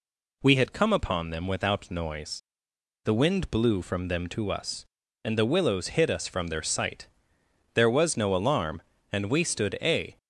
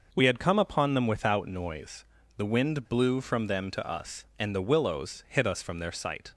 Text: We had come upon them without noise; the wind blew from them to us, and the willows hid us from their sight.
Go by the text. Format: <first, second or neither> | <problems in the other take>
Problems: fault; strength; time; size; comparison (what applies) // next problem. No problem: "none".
second | goes on to say "There was no alarm and we stood a"; strong; from 7.7 s on; 2.4 s long